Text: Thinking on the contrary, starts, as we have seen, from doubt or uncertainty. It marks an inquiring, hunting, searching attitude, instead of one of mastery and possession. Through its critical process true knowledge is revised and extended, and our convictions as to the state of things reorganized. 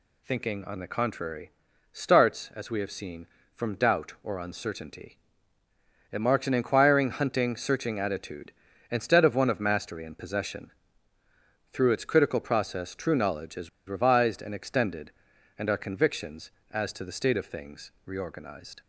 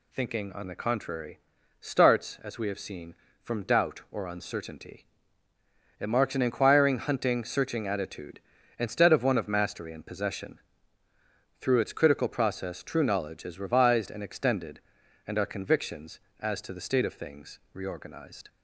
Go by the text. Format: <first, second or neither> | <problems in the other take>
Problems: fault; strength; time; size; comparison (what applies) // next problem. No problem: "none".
second | pauses between "is" and "revised"; slight; at 13.6 s; 0.19 s long // pauses between "things" and "reorganized"; slight; at 17.9 s; 0.16 s long; slight in the second